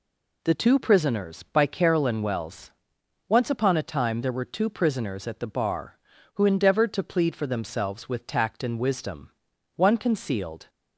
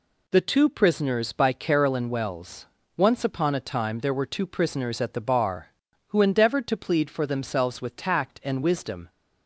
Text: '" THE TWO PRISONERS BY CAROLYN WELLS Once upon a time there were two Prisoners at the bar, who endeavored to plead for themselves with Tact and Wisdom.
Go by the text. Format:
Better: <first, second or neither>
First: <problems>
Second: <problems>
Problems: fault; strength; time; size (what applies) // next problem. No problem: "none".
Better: second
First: pauses between "WELLS" and "Once"; noticeable; at 2.7 s; 0.56 s long // goes on to say "One concealed"; noticeable; from 9.7 s on; 0.94 s long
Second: pauses between "WELLS" and "Once"; slight; at 2.6 s; 0.30 s long